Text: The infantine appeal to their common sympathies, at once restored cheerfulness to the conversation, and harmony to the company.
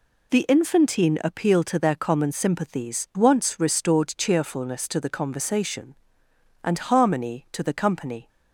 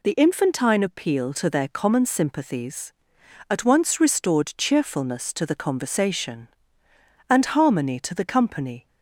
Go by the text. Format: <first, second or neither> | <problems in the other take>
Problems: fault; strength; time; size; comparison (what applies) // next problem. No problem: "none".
second | skips "at"; at 3.1 s